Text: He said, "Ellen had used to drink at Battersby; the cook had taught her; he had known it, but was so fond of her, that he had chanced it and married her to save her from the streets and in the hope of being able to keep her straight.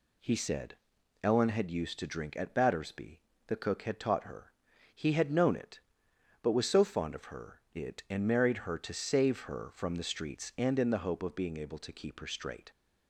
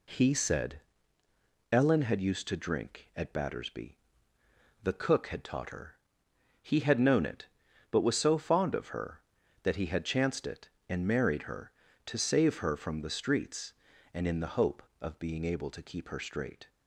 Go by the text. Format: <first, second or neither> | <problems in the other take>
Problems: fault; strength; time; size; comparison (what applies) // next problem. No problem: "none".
second | skips "that he had chanced"; at 7.6 s